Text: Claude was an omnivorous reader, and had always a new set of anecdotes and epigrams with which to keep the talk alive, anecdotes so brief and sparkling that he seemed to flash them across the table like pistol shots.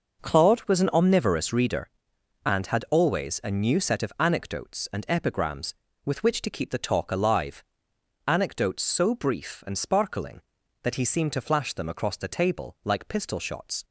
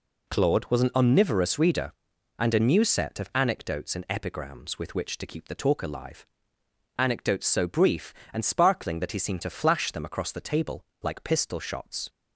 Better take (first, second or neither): first